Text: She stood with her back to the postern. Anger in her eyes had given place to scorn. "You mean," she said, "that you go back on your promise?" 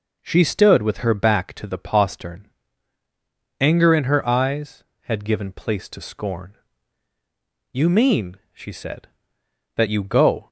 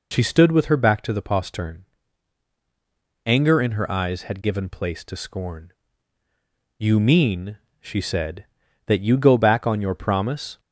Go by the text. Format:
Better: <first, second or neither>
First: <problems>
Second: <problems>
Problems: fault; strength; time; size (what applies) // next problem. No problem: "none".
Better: second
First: stops before "back on your promise"; at 10.4 s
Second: none